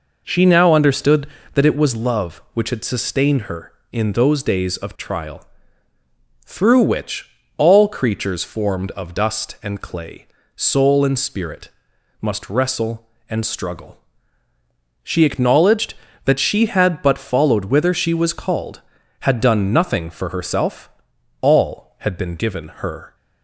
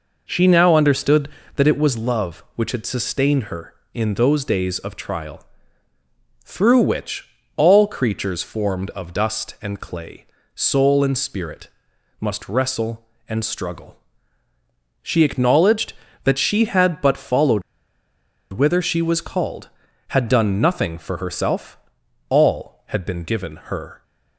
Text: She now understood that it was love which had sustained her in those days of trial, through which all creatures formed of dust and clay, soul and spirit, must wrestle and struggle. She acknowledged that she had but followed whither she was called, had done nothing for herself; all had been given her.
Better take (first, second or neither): first